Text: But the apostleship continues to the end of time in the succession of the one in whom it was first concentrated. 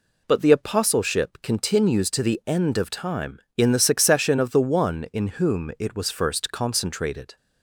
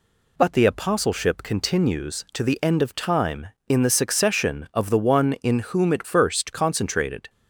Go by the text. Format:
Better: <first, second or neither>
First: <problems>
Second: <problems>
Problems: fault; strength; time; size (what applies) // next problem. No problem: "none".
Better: first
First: none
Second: skips "was"; at 6.0 s